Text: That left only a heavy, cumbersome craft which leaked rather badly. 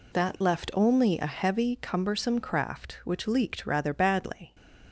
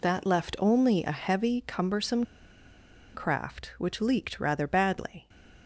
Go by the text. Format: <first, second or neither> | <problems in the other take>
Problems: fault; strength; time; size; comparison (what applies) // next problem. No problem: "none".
first | pauses between "cumbersome" and "craft"; noticeable; at 2.2 s; 0.89 s long